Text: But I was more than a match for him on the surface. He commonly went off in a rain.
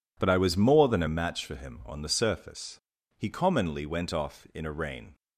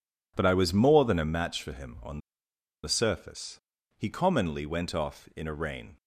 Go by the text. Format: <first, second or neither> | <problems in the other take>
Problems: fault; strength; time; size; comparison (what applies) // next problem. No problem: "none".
first | pauses between "on" and "the"; noticeable; at 2.1 s; 0.65 s long